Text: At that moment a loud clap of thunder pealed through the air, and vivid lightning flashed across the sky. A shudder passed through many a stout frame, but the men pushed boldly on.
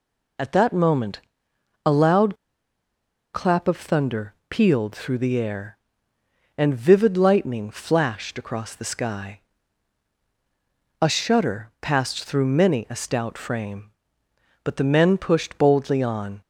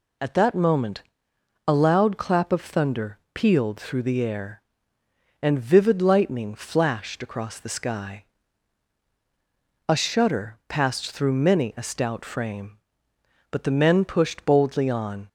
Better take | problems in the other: second | pauses between "moment" and "a"; noticeable; at 1.1 s; 0.66 s long; noticeable in the second // pauses between "loud" and "clap"; at 2.3 s; 0.98 s long // pauses between "thunder" and "pealed"; slight; at 4.3 s; 0.16 s long; slight in the second

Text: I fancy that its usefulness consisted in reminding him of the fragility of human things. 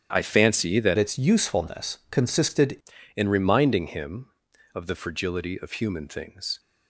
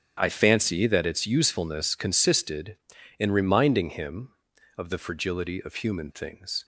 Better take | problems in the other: second | starts louder than the rest; strong; until 1.1 s; 9.5 dB; strong in the second // changes voice from "its" to "consisted"; from 0.9 to 2.7 s; 1.8 s long

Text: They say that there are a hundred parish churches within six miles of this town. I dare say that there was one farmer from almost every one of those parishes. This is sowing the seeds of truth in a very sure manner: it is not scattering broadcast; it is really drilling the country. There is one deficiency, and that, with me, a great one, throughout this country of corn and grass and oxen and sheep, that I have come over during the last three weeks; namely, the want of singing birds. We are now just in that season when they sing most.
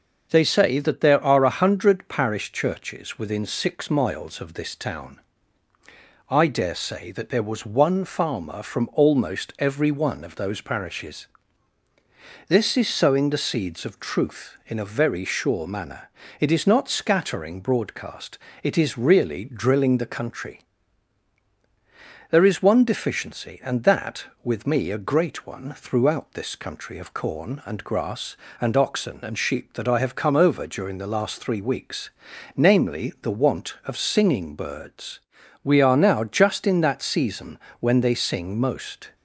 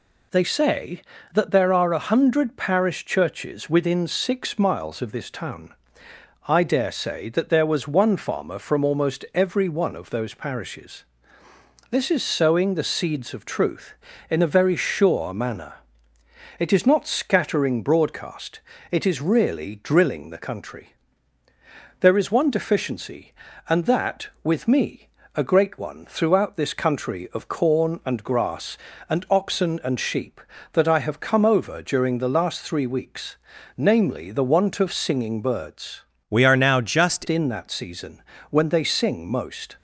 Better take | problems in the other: first | changes voice from "We" to "just"; from 36.2 to 37.2 s; 1.0 s long // pauses between "season" and "when"; slight; at 38.2 s; 0.26 s long; slight in the first

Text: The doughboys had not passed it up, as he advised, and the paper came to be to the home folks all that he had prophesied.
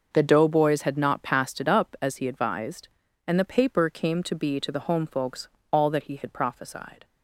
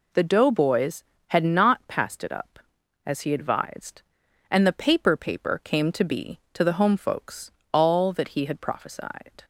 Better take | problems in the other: first | says "paper" twice; at 5.1 s // pauses between "folks" and "all"; slight; at 7.5 s; 0.20 s long; slight in the first

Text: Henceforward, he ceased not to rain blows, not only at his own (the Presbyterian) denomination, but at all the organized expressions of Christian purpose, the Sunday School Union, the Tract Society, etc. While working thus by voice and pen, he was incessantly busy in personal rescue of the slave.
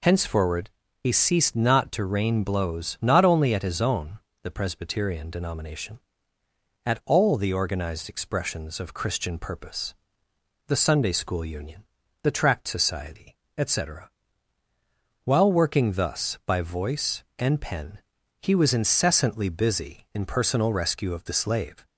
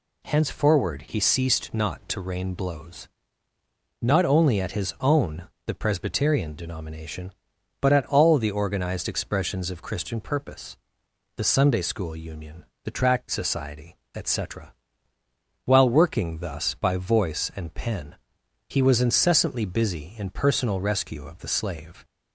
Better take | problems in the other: second | skips "but"; at 6.4 s

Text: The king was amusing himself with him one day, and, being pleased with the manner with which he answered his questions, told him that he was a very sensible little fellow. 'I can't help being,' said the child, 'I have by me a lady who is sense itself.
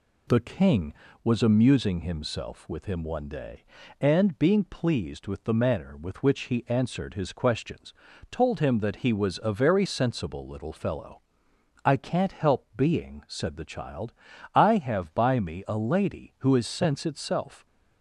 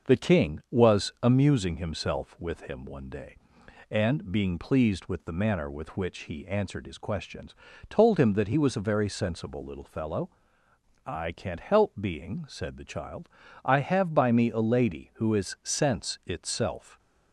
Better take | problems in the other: neither | none

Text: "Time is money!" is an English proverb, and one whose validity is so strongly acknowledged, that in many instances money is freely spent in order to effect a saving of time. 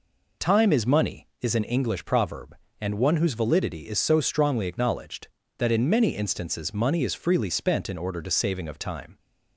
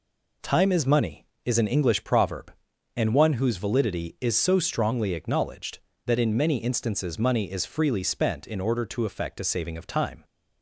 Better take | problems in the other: second | skips "effect a"; at 8.3 s

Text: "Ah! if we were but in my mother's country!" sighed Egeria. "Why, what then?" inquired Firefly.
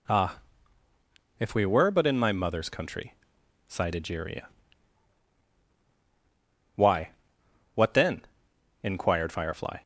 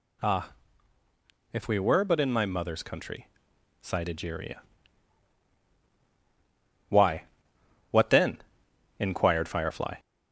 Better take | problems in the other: first | gets louder; slight; throughout; 3 dB

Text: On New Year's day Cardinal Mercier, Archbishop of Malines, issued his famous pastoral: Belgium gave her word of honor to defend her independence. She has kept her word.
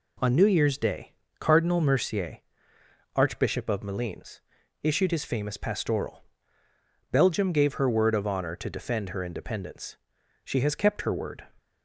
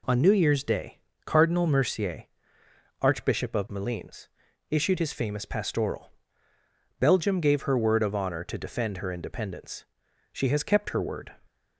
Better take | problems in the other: neither | pauses between "day" and "Cardinal"; slight; the same in both

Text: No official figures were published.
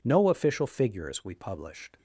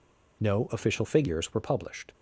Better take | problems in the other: second | says "we" for "were"; at 1.2 s

